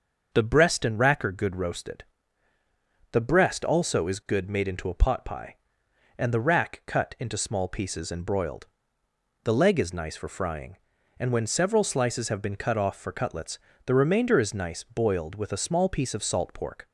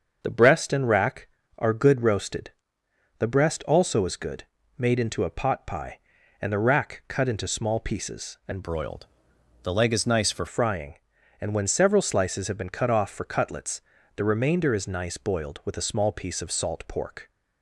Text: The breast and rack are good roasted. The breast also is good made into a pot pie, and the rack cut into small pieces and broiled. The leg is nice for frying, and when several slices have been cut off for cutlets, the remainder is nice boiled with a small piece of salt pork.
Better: first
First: starts louder than the rest; until 1.3 s; 6.5 dB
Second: starts louder than the rest; until 1.2 s; 6.5 dB // pauses between "good" and "made"; slight; at 4.4 s; 0.36 s long // changes voice from "broiled" to "for"; from 8.6 to 10.4 s; 1.8 s long

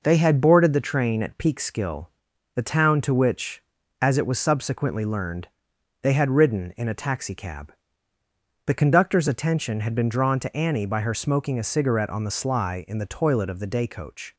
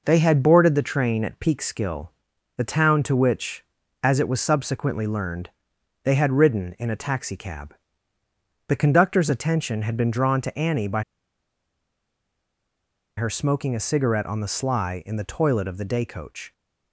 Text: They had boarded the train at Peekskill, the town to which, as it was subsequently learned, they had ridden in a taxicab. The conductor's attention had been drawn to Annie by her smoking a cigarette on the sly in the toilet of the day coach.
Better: first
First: none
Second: pauses between "by" and "her"; strong; at 11.0 s; 2.1 s long

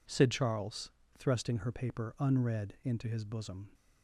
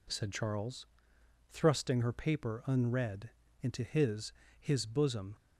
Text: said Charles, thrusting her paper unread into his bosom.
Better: first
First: none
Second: pauses between "unread" and "into"; slight; at 3.3 s; 0.32 s long // says "his" twice; at 4.5 s

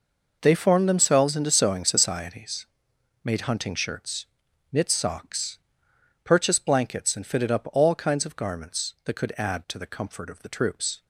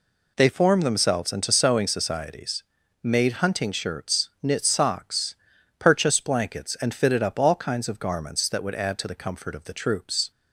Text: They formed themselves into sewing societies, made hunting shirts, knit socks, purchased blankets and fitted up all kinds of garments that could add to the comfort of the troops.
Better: first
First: none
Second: says "would" for "could"; at 8.6 s

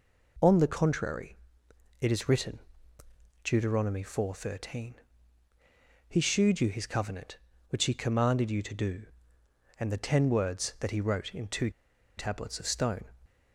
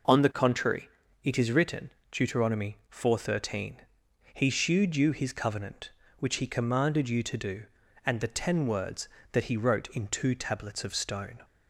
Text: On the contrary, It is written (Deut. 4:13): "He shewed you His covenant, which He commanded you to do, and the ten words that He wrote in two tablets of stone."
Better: second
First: pauses between "two" and "tablets"; noticeable; at 11.7 s; 0.46 s long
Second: none

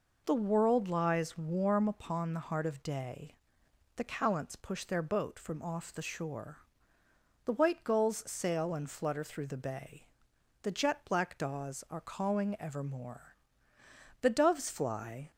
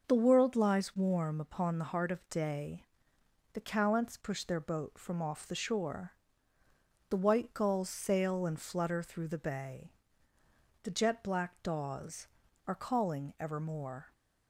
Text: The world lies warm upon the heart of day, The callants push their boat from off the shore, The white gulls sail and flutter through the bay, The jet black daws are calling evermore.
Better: second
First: goes on to say "The doves fly"; noticeable; from 14.2 s on; 1.1 s long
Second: none

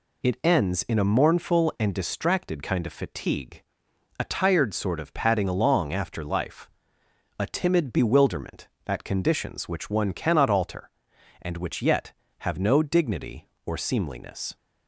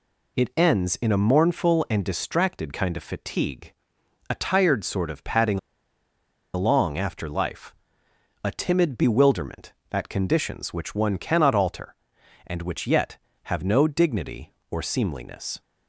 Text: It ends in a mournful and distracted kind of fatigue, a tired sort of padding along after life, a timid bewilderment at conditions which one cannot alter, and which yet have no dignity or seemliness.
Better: first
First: none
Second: pauses between "padding" and "along"; noticeable; at 5.5 s; 0.96 s long

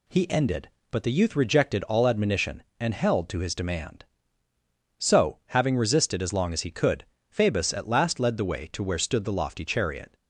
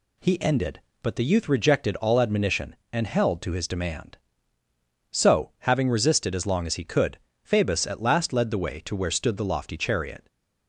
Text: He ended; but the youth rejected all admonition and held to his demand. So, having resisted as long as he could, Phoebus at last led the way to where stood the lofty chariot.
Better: neither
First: none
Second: none

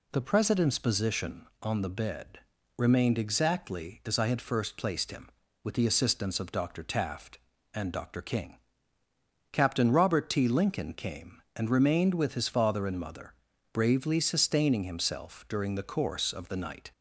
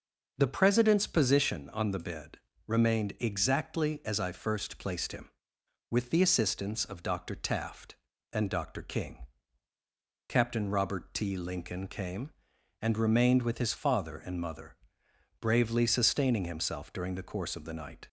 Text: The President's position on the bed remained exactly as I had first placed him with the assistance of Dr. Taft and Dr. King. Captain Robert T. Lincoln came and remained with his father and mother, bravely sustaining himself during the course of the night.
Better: first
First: pauses between "bed" and "remained"; slight; at 2.4 s; 0.36 s long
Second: pauses between "bed" and "remained"; slight; at 2.3 s; 0.28 s long // skips "had"; at 4.3 s

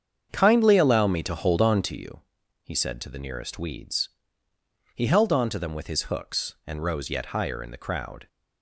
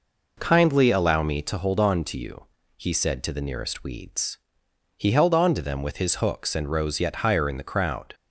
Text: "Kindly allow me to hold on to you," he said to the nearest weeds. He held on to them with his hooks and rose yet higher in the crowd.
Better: second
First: starts louder than the rest; strong; until 2.0 s; 7.5 dB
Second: none

